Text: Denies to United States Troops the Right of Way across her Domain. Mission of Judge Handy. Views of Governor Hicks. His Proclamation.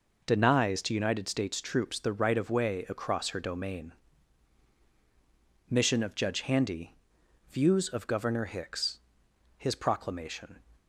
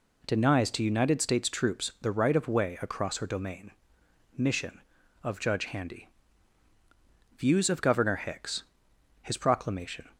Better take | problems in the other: neither | none

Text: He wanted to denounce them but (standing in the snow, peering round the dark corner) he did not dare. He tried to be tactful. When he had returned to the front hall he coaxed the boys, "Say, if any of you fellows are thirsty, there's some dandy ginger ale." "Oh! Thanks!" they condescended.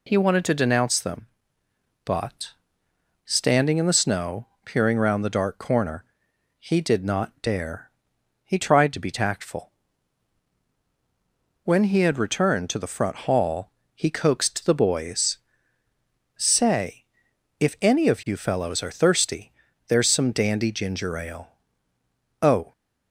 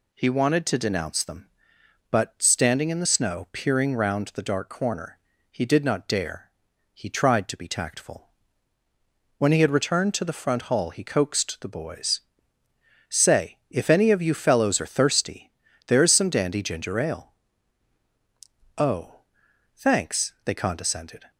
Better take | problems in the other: second | pauses between "hall" and "he"; slight; at 13.6 s; 0.26 s long // stops before "Thanks they condescended"; at 22.7 s

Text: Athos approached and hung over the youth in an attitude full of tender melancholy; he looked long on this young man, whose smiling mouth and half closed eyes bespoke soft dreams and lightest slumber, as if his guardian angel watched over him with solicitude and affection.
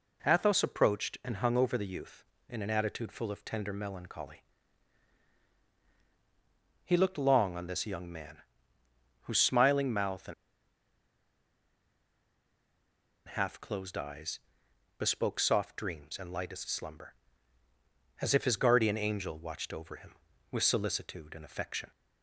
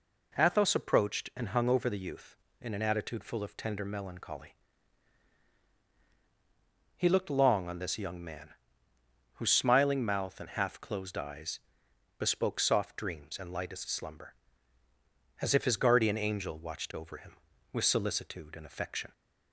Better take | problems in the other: second | pauses between "and" and "half"; strong; at 10.3 s; 2.9 s long // pauses between "eyes" and "bespoke"; noticeable; at 14.3 s; 0.58 s long; noticeable in the second

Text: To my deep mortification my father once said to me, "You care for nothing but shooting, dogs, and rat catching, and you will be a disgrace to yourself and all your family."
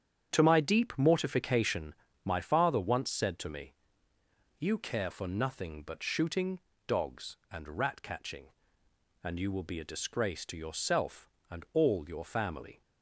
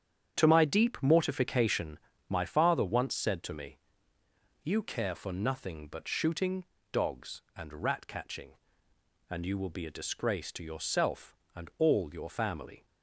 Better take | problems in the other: neither | starts louder than the rest; strong; the same in both // pauses between "mortification" and "my"; slight; the same in both

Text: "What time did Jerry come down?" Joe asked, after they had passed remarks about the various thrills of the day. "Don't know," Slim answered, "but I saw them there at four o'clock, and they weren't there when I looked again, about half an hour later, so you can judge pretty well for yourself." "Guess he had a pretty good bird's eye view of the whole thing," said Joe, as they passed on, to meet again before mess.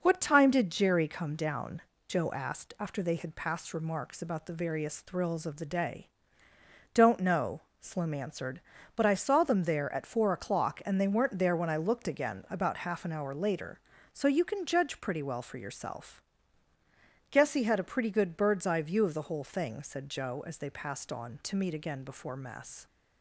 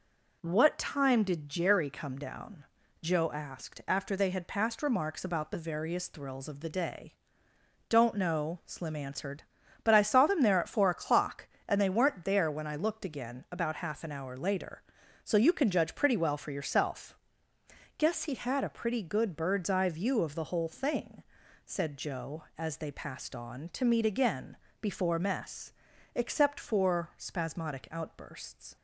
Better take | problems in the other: first | pauses between "again" and "before"; slight; at 24.5 s; 0.26 s long // goes on to say "Except for spasmodic outbursts"; strong; from 26.1 s on; 2.6 s long

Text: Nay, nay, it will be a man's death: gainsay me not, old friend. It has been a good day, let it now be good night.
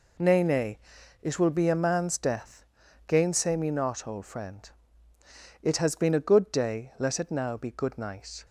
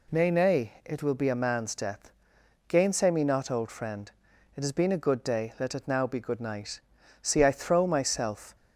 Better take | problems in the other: first | goes on to say "See I throw myself"; from 7.2 s on; 1.3 s long

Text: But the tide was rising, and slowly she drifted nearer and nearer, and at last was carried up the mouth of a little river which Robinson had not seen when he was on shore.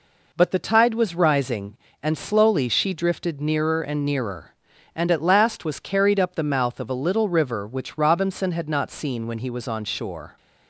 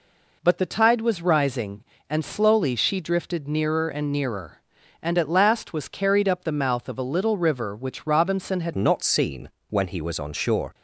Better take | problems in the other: first | changes voice at "not"; from 8.7 s on; 2.0 s long // pauses between "seen" and "when"; slight; at 9.4 s; 0.20 s long

